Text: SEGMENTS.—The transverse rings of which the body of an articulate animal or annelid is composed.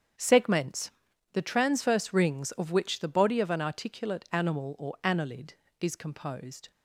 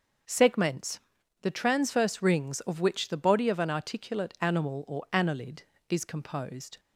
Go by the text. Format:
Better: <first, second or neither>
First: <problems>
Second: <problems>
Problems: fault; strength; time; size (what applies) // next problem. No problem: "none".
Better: second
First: gets quieter; strong; throughout; 12 dB // starts louder than the rest; strong; until 1.6 s; 8 dB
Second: starts louder than the rest; until 1.7 s; 6.5 dB